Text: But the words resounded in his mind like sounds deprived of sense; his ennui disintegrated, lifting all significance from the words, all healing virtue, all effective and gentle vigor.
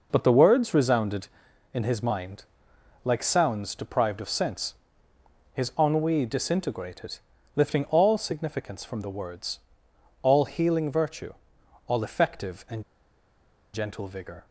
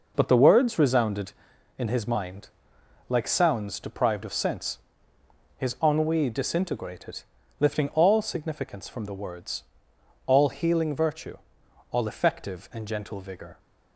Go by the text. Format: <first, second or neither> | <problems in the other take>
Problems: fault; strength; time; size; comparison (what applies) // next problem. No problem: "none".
second | pauses between "mind" and "like"; noticeable; at 2.4 s; 0.58 s long; noticeable in the second // pauses between "and" and "gentle"; noticeable; at 12.8 s; 0.90 s long